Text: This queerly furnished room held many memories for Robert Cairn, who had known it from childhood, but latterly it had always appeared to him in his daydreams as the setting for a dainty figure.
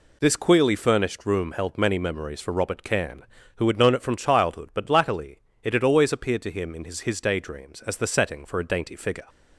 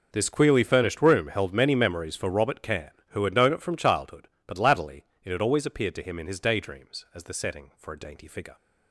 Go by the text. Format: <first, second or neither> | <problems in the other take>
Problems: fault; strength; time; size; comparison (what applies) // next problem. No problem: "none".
second | pauses between "latterly" and "it"; slight; at 5.3 s; 0.22 s long; slight in the second // says "his" twice; at 7.0 s